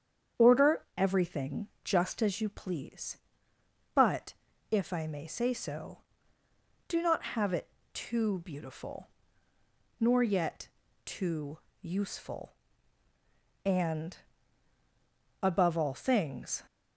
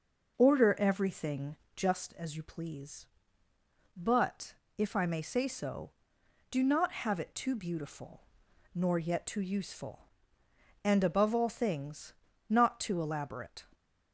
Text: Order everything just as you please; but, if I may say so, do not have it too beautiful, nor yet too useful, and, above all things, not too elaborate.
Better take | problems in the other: second | starts louder than the rest; strong; until 1.5 s; 8 dB // pauses between "Order" and "everything"; slight; at 0.8 s; 0.16 s long // pauses between "everything" and "just"; slight; at 1.6 s; 0.16 s long; slight in the second // pauses between "it" and "too"; slight; at 7.6 s; 0.24 s long // pauses between "yet" and "too"; at 10.6 s; 0.38 s long // pauses between "too" and "useful"; slight; at 11.5 s; 0.22 s long // stops before "not too elaborate"; at 16.6 s

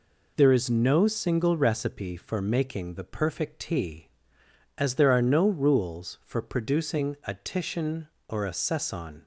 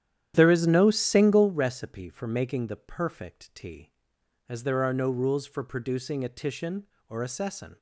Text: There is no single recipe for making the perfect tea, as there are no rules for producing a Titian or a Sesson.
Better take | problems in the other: first | starts louder than the rest; strong; until 1.5 s; 10.5 dB

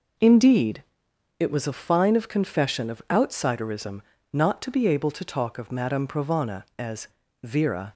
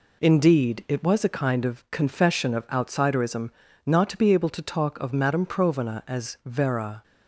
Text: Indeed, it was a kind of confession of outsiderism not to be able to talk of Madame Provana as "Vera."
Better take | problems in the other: second | says "fine" for "kind"; at 1.7 s // pauses between "outsiderism" and "not"; slight; at 4.0 s; 0.32 s long; slight in the second // pauses between "as" and "Vera"; slight; at 7.0 s; 0.36 s long

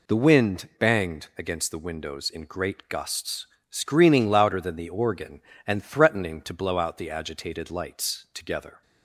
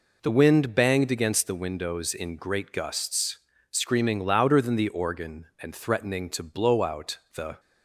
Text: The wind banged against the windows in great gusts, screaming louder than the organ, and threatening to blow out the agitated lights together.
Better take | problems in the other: first | pauses between "out" and "the"; slight; at 7.1 s; 0.20 s long // stops before "agitated lights together"; at 7.5 s

